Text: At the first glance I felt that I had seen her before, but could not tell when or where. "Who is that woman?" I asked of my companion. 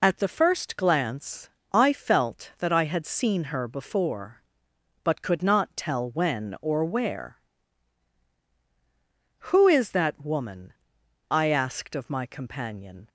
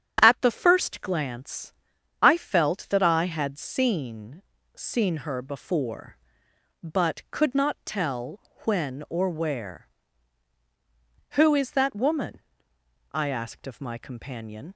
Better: first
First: pauses between "glance" and "I"; slight; at 1.4 s; 0.24 s long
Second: starts louder than the rest; strong; until 1.2 s; 8.5 dB // pauses between "glance" and "I"; noticeable; at 1.7 s; 0.50 s long // says "seen" twice; at 4.7 s // pauses between "tell" and "when"; slight; at 8.4 s; 0.24 s long

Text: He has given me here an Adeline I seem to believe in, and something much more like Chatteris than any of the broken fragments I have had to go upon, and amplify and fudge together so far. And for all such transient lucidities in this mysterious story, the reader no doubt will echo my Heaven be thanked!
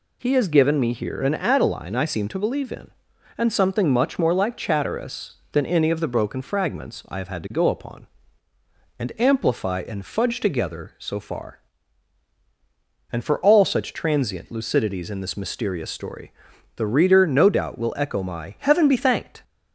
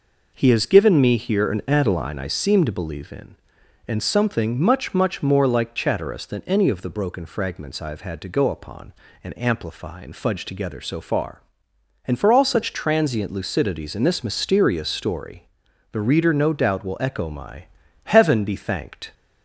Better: first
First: none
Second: says "much" twice; at 4.9 s // pauses between "my" and "Heaven"; at 17.6 s; 0.40 s long

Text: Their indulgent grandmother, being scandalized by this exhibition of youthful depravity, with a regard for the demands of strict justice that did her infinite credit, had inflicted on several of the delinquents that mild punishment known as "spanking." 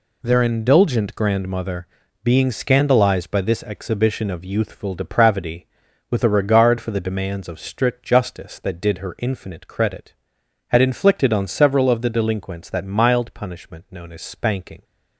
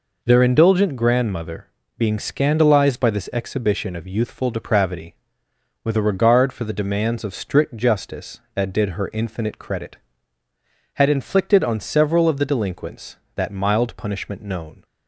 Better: first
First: none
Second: stops before "as spanking"; at 14.8 s

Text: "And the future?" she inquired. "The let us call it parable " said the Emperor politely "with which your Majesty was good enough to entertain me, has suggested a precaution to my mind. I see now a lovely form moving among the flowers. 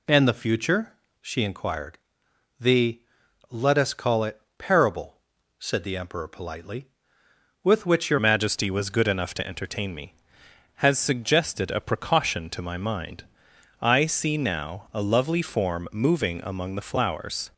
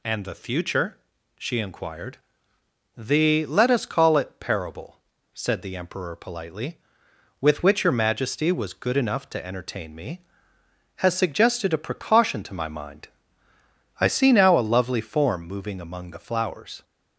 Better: second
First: pauses between "The" and "let"; noticeable; at 3.0 s; 0.48 s long // pauses between "it" and "parable"; slight; at 4.3 s; 0.20 s long // changes voice at "Majesty"; from 8.1 s on; 9.3 s long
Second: none

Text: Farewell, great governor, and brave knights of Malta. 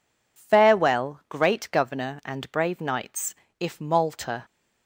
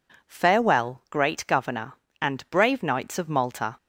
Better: second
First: says "if" for "of"; at 3.5 s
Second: none

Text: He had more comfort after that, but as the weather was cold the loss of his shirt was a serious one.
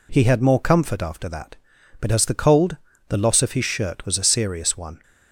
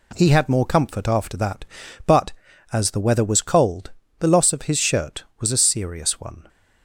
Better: second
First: skips "weather was"; at 2.3 s // pauses between "cold" and "the"; slight; at 2.7 s; 0.34 s long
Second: pauses between "cold" and "the"; slight; at 3.9 s; 0.28 s long

